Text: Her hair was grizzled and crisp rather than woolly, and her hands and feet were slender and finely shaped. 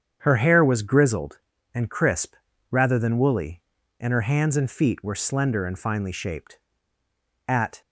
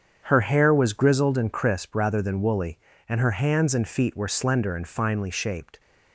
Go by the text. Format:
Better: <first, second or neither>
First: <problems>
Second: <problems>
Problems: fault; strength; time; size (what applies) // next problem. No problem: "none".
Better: second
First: starts louder than the rest; strong; until 1.2 s; 8 dB // pauses between "crisp" and "rather"; slight; at 2.3 s; 0.34 s long // goes on to say "At"; slight; from 7.4 s on; 0.34 s long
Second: starts louder than the rest; strong; until 1.2 s; 8 dB